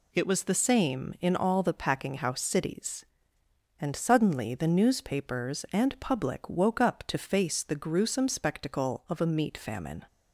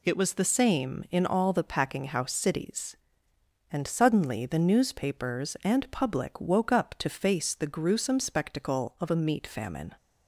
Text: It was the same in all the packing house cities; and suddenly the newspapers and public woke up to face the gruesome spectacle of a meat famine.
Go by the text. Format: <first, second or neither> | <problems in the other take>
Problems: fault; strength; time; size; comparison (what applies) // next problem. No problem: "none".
neither | none